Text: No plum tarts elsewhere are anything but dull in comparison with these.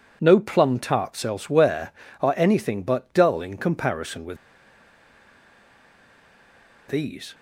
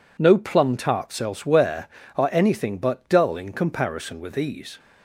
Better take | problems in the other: second | pauses between "with" and "these"; strong; at 4.3 s; 2.5 s long

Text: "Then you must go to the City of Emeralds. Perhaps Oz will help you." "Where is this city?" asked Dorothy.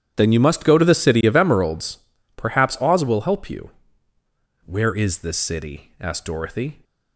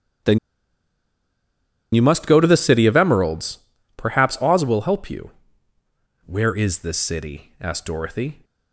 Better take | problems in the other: first | starts louder than the rest; strong; until 2.7 s; 10 dB; strong in the first // pauses between "Then" and "you"; strong; at 0.3 s; 1.5 s long

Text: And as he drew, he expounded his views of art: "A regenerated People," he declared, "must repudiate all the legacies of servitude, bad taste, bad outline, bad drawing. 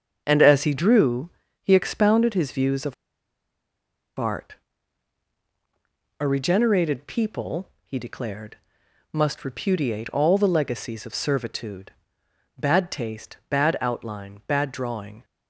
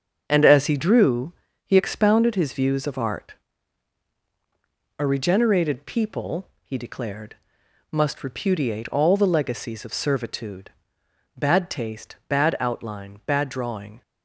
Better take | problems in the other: second | starts louder than the rest; until 1.2 s; 6.5 dB; also in the second // pauses between "of" and "art"; at 2.9 s; 1.2 s long

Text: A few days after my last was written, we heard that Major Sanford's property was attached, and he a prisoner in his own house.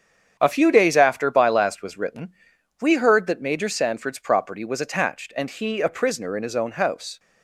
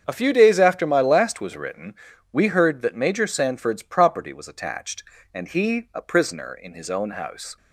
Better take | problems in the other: second | starts louder than the rest; strong; until 1.4 s; 8 dB; strong in the second // says "by" for "my"; at 1.3 s

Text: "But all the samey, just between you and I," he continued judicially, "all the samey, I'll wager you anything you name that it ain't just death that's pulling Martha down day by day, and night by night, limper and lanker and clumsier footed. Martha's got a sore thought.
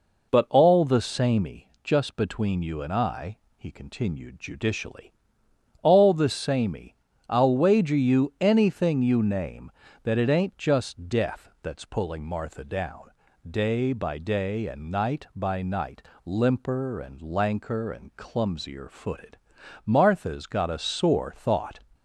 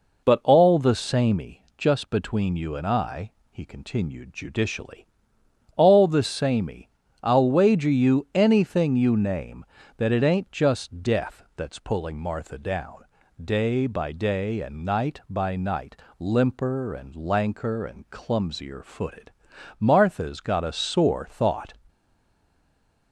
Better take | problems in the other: first | pauses between "down" and "day"; at 13.0 s; 0.40 s long; also in the first // stays silent after the last word; noticeable; from 21.8 s on; 1.3 s long

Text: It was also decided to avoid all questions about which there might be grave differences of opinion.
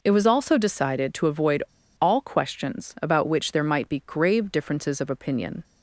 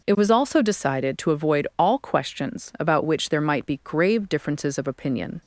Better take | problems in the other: second | pauses between "avoid" and "all"; at 1.6 s; 0.38 s long

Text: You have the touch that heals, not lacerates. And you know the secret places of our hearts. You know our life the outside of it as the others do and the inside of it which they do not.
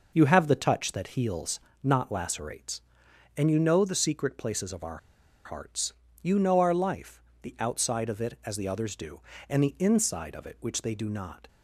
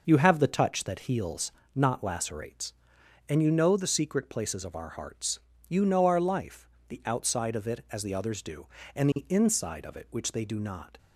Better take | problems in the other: second | pauses between "our" and "hearts"; noticeable; at 4.9 s; 0.47 s long // pauses between "life" and "the"; slight; at 7.2 s; 0.20 s long; slight in the second

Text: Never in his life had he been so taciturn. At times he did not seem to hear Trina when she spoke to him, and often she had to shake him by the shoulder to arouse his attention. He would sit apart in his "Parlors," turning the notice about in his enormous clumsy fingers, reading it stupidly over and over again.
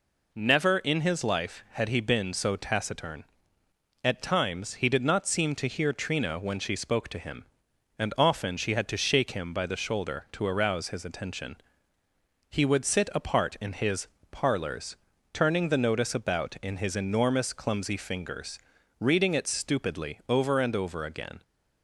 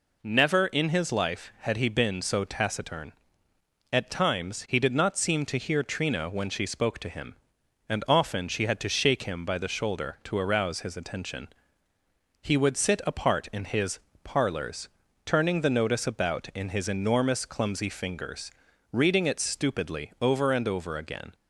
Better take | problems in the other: neither | pauses between "his" and "Parlors"; slight; the same in both

